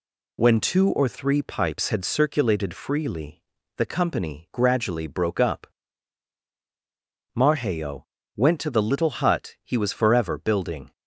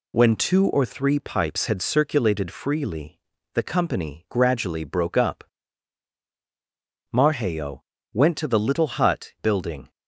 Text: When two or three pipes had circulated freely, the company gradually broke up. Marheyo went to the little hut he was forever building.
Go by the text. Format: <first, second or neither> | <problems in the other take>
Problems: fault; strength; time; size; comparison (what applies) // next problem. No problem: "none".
first | pauses between "Marheyo" and "went"; slight; at 7.8 s; 0.32 s long; slight in the first // skips "he was forever"; at 9.3 s